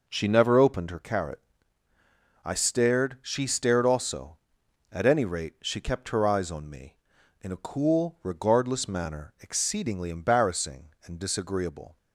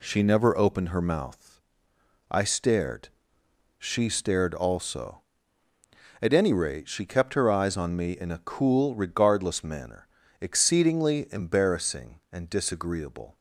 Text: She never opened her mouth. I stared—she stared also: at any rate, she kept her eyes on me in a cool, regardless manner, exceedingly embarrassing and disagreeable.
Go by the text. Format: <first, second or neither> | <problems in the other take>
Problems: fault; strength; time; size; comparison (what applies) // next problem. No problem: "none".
second | says "carrot" for "mouth"; at 0.9 s